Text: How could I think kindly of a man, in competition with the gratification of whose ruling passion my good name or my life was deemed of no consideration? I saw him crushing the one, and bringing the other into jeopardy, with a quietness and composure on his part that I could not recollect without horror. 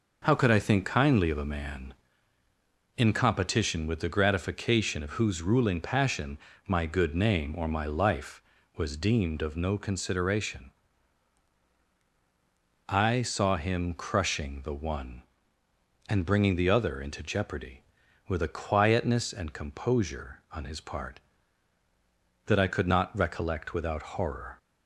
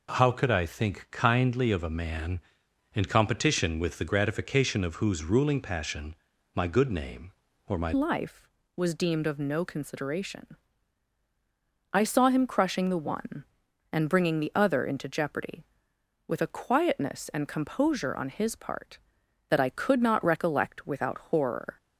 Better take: first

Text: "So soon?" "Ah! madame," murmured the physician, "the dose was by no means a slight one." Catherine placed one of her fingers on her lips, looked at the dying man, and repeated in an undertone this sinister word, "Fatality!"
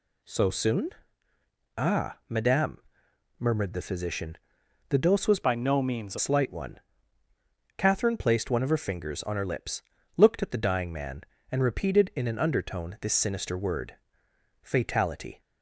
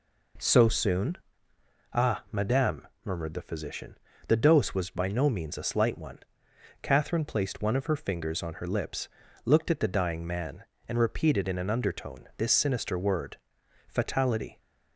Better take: second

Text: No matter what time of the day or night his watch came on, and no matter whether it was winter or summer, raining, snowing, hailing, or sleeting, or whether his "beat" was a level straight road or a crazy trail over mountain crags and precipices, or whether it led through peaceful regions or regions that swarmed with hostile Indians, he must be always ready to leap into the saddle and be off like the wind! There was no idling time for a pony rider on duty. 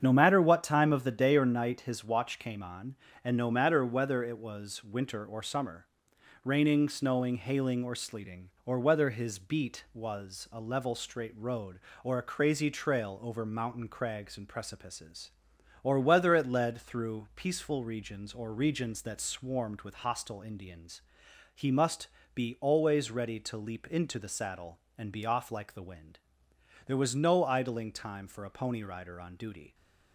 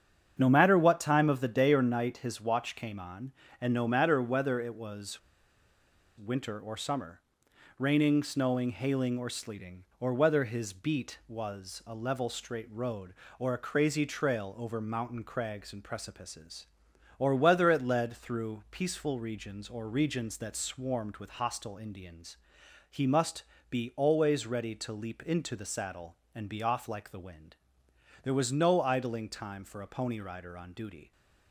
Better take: first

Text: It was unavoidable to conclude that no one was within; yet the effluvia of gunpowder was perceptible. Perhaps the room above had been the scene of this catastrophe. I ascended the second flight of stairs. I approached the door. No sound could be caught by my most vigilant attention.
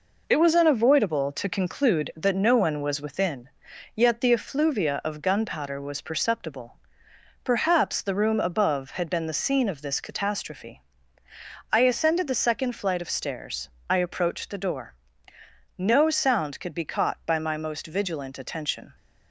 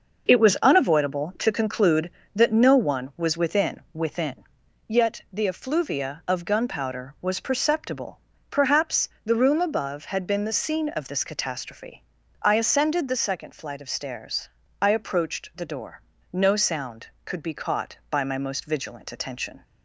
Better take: first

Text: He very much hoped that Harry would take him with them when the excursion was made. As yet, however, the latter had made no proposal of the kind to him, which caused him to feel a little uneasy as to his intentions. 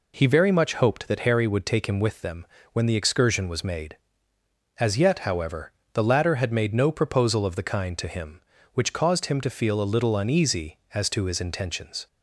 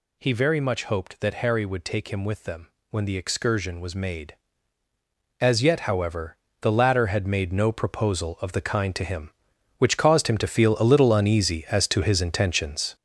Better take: first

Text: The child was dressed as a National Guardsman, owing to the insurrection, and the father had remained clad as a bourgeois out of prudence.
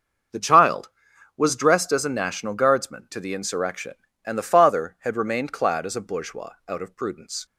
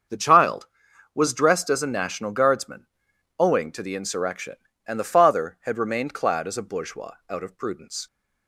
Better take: second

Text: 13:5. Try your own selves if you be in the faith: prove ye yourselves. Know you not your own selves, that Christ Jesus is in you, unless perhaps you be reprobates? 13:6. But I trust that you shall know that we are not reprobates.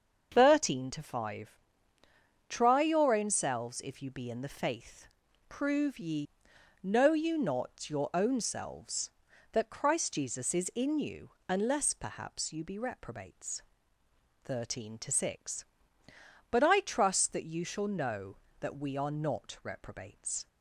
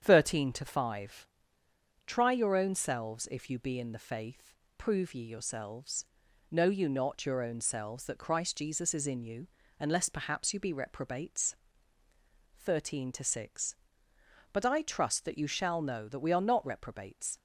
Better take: second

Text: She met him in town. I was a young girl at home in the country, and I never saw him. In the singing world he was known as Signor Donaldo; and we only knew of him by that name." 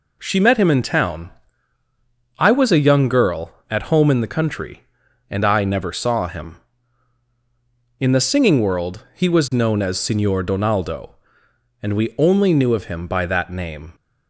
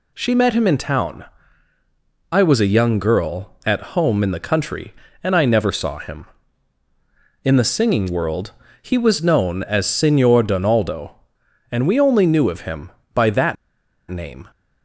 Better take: first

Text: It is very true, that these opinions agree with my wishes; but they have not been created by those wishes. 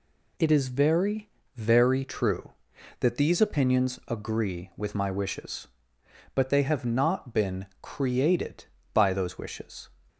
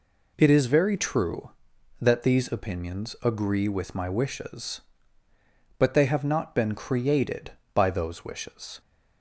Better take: second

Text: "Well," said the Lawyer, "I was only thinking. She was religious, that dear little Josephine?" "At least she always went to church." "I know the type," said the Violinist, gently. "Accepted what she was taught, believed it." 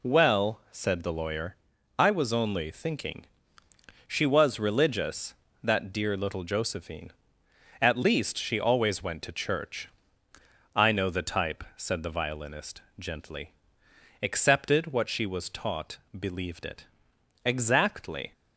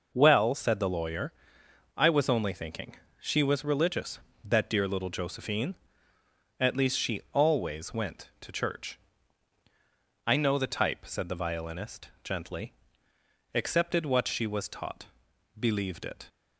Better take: second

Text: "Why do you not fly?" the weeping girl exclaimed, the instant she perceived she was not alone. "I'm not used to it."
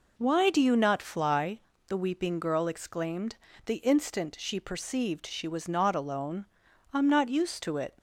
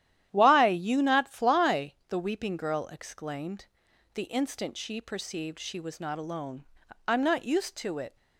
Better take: first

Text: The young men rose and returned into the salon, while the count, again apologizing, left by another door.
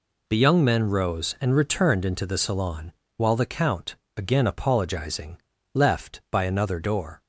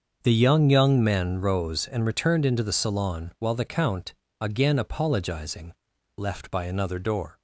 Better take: first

